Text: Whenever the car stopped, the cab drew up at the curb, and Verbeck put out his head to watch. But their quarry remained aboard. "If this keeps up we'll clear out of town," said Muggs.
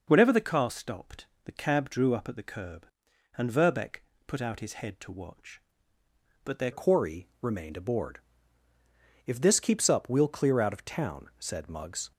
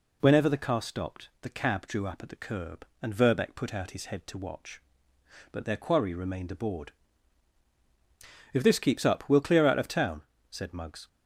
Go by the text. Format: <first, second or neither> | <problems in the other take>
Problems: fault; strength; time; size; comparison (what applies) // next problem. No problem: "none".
second | pauses between "Verbeck" and "put"; slight; at 4.0 s; 0.24 s long // changes voice at "quarry"; from 6.7 s on; 5.4 s long // pauses between "quarry" and "remained"; slight; at 7.2 s; 0.16 s long